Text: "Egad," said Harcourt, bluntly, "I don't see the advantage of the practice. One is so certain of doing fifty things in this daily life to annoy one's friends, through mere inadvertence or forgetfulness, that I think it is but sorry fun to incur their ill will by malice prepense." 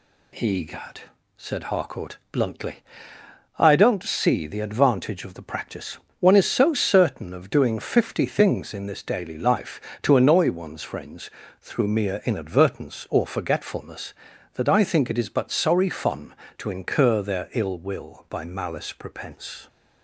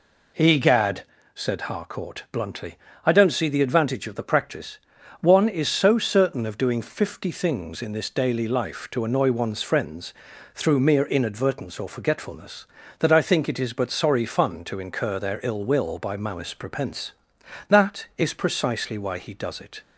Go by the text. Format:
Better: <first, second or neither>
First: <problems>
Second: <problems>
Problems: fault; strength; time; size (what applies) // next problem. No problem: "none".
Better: first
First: none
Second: goes on to say "That is precisely why he does it"; strong; from 17.6 s on; 2.1 s long